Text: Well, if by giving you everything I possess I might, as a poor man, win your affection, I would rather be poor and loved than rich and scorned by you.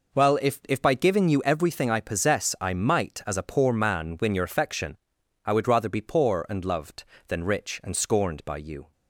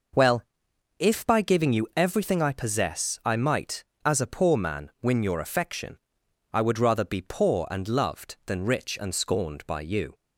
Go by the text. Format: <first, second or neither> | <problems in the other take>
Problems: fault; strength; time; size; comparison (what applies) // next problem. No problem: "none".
second | says "if" twice; at 0.6 s